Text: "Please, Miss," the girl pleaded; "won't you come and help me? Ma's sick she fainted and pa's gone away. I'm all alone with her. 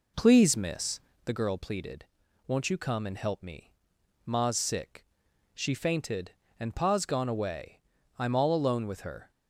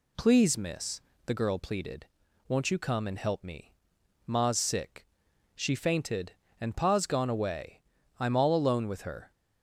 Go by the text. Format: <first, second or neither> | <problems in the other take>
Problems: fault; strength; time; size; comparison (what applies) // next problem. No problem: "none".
second | starts louder than the rest; until 1.2 s; 3.5 dB // pauses between "sick" and "she"; noticeable; at 5.0 s; 0.52 s long; noticeable in the second